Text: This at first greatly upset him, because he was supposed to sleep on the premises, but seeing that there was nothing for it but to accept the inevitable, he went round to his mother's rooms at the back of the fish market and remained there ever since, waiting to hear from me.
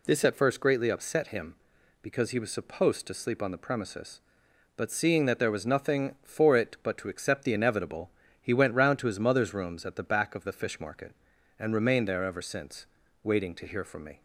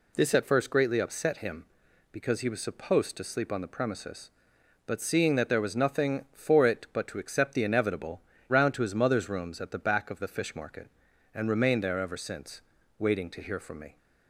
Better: first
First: none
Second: skips "he went"; at 8.3 s

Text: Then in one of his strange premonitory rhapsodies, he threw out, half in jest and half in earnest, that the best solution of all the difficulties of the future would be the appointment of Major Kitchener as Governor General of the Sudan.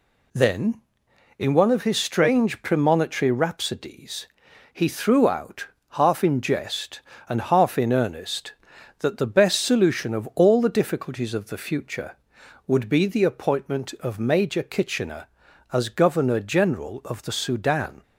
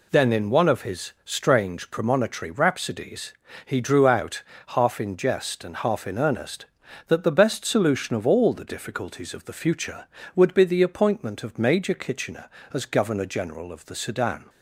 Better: first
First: none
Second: says "drew" for "threw"; at 3.7 s

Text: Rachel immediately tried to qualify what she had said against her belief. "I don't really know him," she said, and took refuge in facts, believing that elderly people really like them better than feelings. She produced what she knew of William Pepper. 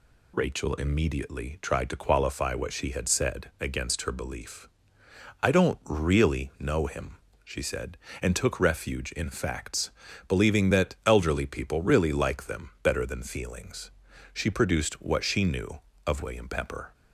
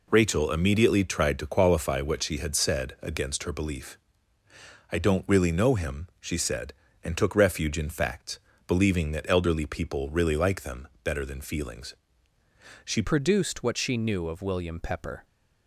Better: first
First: none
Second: pauses between "them" and "better"; slight; at 10.8 s; 0.16 s long // changes voice at "produced"; from 13.0 s on; 2.2 s long

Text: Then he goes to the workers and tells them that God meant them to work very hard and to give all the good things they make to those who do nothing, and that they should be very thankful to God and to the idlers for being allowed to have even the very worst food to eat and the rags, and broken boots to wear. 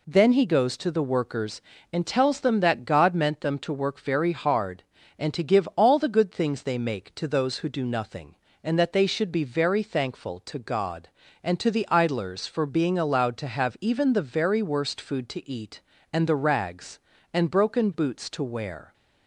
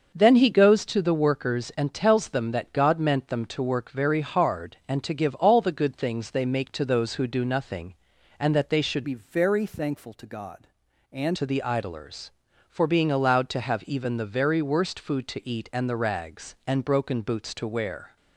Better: first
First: none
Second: starts louder than the rest; until 1.1 s; 6.5 dB // changes voice from "be" to "and"; from 9.0 to 11.3 s; 2.3 s long

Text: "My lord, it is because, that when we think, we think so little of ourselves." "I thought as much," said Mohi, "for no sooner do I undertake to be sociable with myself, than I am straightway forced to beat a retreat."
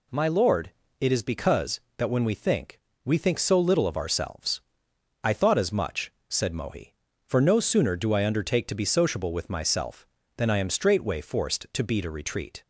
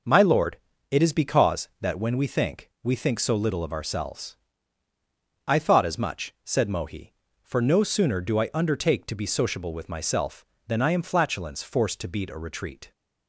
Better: first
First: none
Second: says "flatulence" for "straightway"; at 11.0 s

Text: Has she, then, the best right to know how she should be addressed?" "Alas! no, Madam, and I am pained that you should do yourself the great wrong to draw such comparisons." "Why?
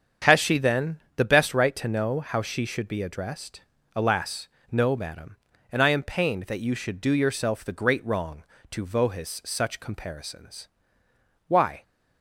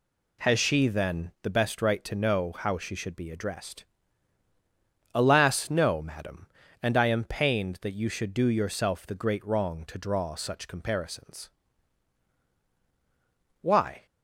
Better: second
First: starts louder than the rest; strong; until 1.4 s; 7.5 dB // says "vohis" for "draw"; at 8.8 s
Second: none

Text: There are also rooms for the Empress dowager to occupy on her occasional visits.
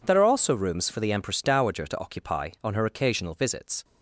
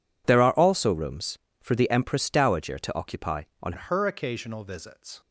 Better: first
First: none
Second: changes voice at "her"; from 3.7 s on; 1.5 s long

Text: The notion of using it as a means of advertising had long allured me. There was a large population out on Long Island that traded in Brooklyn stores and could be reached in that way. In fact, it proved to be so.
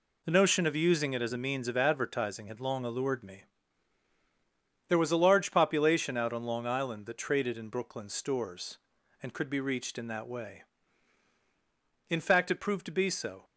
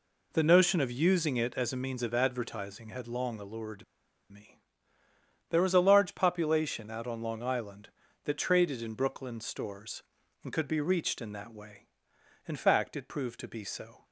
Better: first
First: none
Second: pauses between "allured" and "me"; noticeable; at 3.8 s; 0.46 s long

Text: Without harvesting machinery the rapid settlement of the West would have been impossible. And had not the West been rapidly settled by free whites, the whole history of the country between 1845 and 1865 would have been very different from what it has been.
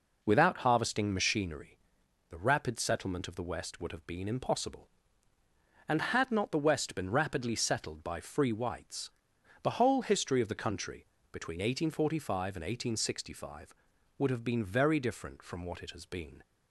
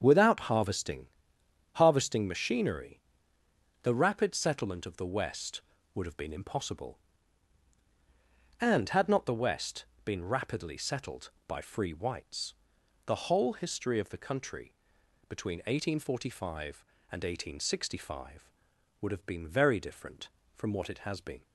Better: first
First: pauses between "machinery" and "the"; noticeable; at 1.7 s; 0.52 s long // pauses between "country" and "between"; slight; at 11.0 s; 0.24 s long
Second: starts louder than the rest; strong; until 1.0 s; 7.5 dB // says "harvesting" twice; at 1.7 s // pauses between "machinery" and "the"; noticeable; at 3.0 s; 0.82 s long // pauses between "West" and "been"; slight; at 9.8 s; 0.20 s long // pauses between "country" and "between"; noticeable; at 14.7 s; 0.56 s long

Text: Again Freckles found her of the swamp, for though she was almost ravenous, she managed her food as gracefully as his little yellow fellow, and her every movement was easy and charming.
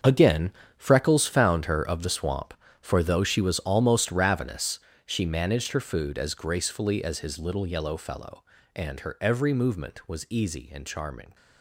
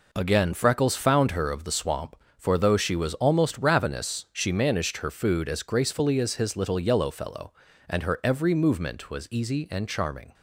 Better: second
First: gets quieter; strong; throughout; 12.5 dB // pauses between "Again" and "Freckles"; slight; at 0.5 s; 0.26 s long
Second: none

